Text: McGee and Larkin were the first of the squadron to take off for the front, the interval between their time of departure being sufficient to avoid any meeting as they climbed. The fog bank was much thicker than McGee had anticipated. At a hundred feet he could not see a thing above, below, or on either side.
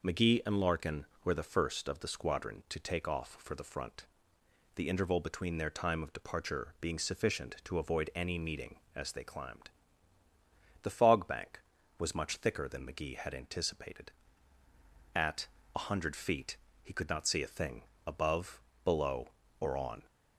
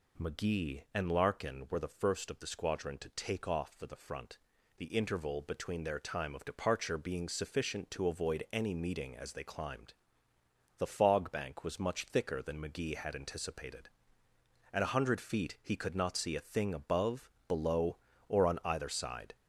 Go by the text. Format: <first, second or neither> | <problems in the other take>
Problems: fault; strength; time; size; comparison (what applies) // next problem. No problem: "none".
second | pauses between "At" and "a"; slight; at 15.4 s; 0.28 s long // pauses between "feet" and "he"; slight; at 16.5 s; 0.26 s long // pauses between "thing" and "above"; slight; at 17.8 s; 0.24 s long // stops before "either side"; at 20.0 s